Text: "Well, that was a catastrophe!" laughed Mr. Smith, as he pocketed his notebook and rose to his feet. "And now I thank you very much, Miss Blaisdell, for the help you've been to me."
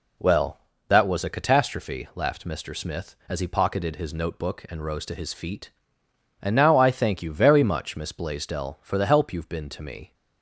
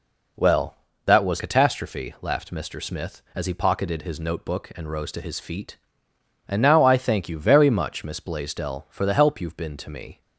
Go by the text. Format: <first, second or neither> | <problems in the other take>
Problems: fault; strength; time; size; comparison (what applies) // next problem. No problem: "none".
first | skips "a"; at 1.3 s